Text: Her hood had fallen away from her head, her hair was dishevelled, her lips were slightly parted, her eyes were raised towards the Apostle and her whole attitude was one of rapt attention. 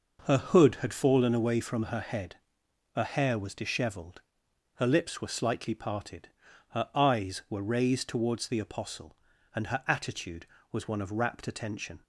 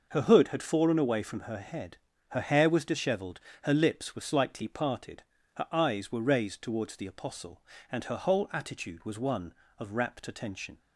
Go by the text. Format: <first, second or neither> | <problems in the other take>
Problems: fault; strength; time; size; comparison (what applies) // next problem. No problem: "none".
second | skips "whole"; at 9.8 s